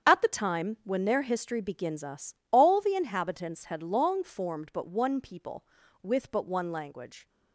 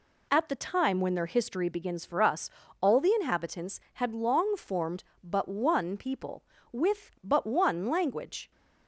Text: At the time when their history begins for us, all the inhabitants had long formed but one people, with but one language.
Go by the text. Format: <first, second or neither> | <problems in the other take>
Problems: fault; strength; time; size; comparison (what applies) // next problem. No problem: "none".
second | starts louder than the rest; strong; until 1.0 s; 8 dB // skips "for"; at 2.0 s